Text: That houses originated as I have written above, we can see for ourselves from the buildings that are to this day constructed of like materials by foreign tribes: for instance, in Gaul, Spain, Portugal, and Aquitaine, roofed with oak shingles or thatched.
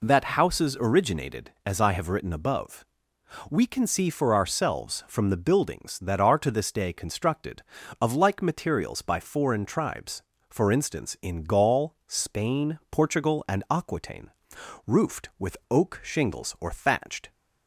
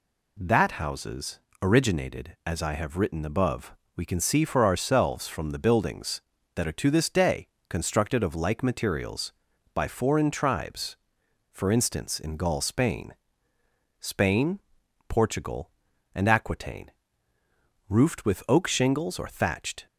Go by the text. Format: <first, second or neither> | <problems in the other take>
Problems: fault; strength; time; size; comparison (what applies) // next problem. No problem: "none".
first | pauses between "houses" and "originated"; slight; at 1.3 s; 0.24 s long // pauses between "day" and "constructed"; slight; at 7.4 s; 0.22 s long // says "Spain" twice; at 14.0 s